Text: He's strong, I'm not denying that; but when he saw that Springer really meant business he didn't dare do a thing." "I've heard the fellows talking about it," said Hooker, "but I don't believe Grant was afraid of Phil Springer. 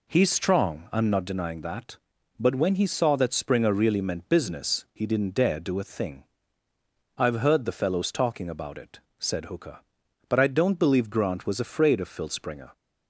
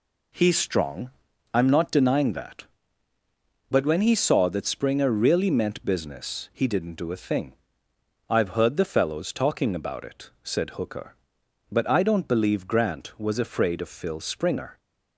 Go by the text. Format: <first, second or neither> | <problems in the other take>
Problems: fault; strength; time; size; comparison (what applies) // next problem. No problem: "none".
first | skips "dare"; at 6.9 s